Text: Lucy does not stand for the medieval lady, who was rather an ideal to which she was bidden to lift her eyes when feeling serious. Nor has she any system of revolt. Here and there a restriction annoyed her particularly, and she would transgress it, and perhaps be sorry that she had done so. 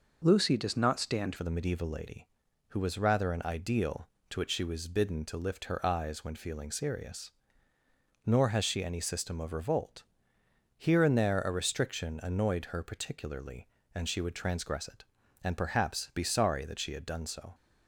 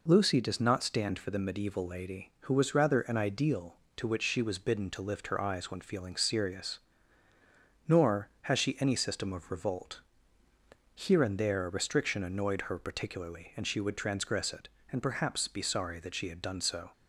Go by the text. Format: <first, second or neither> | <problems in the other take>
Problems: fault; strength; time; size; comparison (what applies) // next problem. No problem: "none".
second | changes voice at "for"; from 1.3 s on; 16.2 s long